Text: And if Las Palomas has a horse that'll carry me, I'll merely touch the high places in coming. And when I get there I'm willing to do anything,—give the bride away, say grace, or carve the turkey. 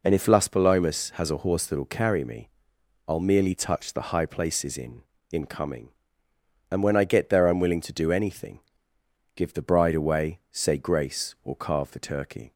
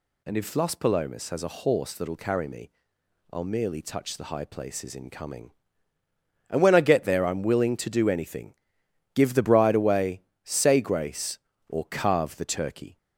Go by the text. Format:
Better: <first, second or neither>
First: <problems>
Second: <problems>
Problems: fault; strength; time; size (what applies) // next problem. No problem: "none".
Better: second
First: says "in" twice; at 5.3 s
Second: none